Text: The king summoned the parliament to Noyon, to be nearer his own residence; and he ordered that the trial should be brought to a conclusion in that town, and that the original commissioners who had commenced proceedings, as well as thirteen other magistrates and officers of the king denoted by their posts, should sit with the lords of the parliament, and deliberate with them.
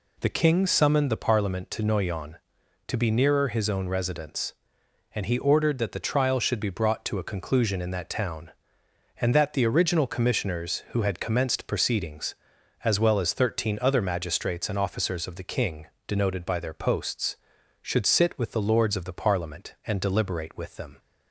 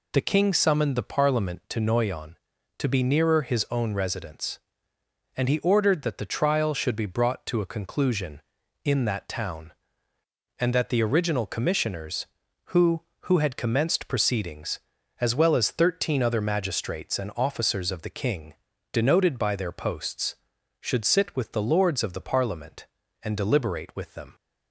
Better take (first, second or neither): first